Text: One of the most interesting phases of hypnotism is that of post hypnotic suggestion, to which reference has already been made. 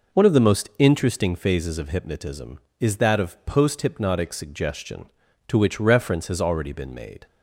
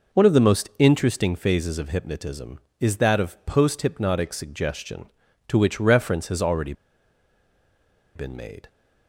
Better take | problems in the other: first | pauses between "already" and "been"; strong; at 6.7 s; 1.4 s long

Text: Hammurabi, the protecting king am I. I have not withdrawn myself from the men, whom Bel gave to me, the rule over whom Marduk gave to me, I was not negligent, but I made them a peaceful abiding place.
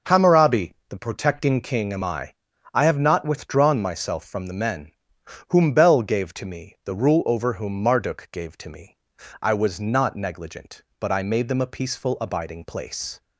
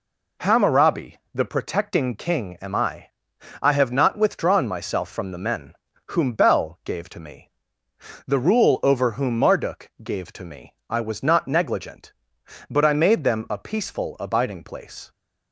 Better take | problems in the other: neither | none

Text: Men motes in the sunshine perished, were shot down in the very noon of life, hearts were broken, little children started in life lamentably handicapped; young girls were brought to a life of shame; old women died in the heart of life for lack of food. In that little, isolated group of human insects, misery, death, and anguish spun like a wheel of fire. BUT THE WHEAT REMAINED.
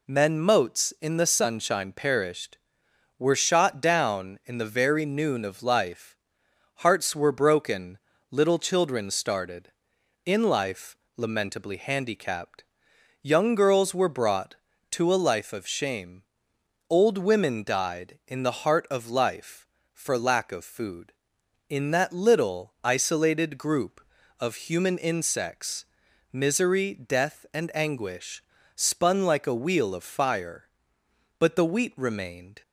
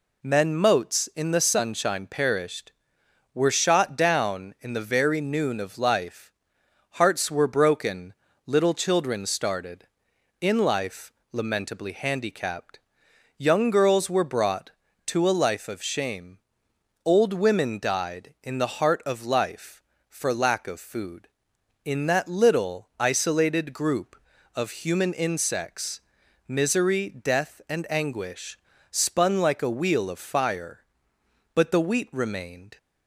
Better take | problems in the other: neither | pauses between "life" and "lamentably"; slight; the same in both // pauses between "anguish" and "spun"; slight; the same in both

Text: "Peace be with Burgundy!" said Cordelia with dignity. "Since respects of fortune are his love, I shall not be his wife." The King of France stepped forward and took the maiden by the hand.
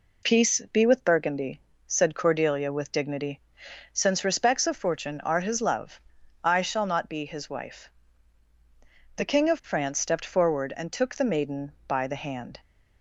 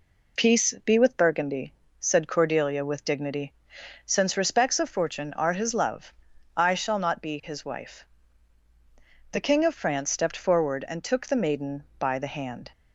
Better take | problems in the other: neither | none

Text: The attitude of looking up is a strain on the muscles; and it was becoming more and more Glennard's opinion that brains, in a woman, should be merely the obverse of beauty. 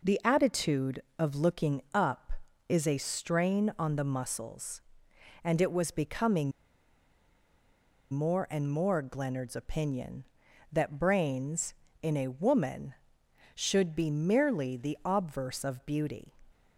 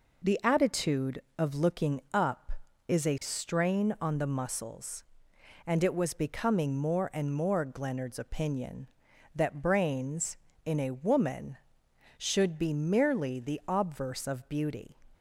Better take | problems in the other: second | pauses between "becoming" and "more"; strong; at 6.5 s; 1.6 s long

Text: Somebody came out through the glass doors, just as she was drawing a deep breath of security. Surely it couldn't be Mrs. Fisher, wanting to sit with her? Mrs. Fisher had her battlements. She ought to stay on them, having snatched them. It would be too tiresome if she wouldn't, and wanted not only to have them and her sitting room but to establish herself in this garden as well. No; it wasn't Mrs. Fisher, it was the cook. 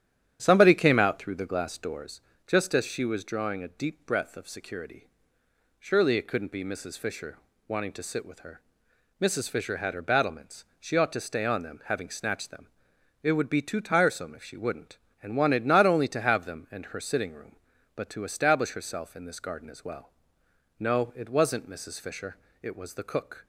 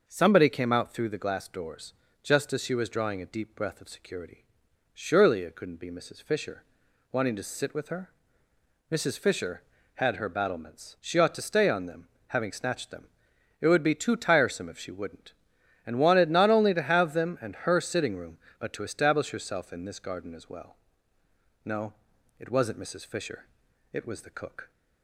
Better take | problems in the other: second | starts louder than the rest; strong; until 2.1 s; 9.5 dB

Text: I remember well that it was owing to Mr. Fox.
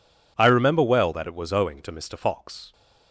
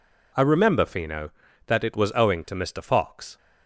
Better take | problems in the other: first | says "fino" for "well"; at 0.8 s

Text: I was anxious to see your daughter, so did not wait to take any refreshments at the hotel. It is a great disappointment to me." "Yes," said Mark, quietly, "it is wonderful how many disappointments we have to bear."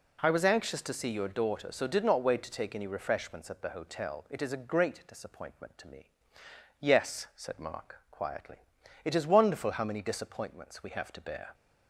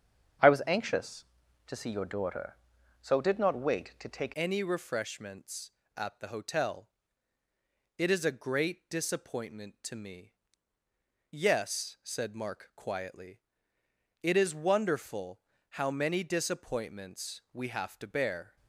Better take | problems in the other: first | starts louder than the rest; strong; until 1.8 s; 7.5 dB // changes voice at "any"; from 4.3 s on; 14.2 s long // pauses between "wonderful" and "how"; slight; at 15.4 s; 0.30 s long

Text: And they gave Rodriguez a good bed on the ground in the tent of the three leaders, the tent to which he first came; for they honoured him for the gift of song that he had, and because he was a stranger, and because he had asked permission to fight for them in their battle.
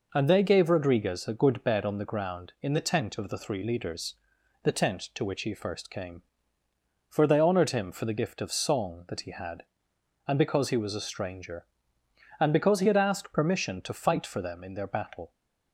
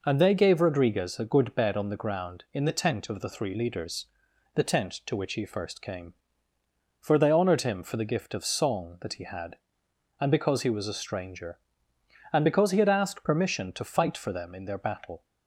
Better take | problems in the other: neither | none

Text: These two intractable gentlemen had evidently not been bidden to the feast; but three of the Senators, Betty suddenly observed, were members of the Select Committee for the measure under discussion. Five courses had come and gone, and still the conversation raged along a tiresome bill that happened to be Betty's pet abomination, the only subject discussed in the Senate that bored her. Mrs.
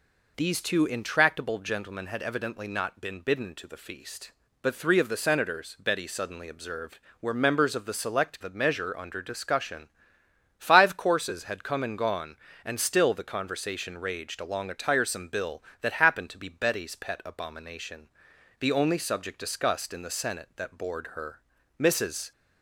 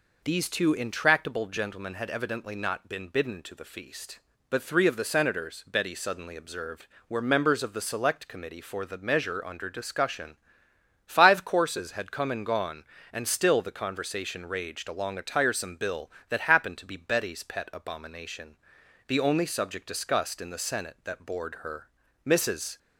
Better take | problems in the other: second | skips "Committee for"; at 8.4 s

